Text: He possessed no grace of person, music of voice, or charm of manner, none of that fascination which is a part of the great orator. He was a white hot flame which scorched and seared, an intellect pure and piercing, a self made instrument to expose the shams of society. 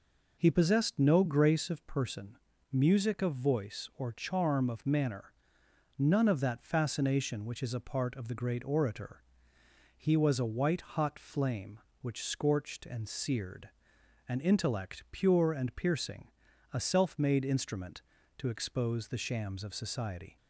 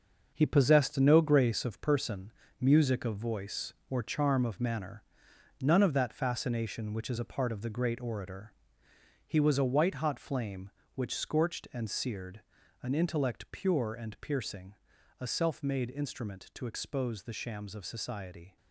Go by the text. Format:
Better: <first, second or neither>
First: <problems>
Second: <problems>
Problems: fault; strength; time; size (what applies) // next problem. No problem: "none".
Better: first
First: none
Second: gets quieter; strong; throughout; 7.5 dB